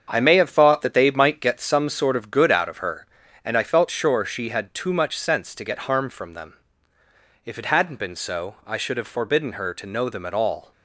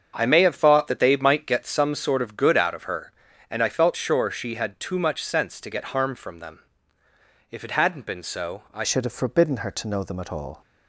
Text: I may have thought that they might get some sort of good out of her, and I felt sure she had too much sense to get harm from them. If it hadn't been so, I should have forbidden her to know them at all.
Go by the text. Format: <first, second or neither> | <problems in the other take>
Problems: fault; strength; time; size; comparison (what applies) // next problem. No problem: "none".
first | starts louder than the rest; until 1.1 s; 7 dB; strong in the first // changes voice at "should"; from 8.8 s on; 1.8 s long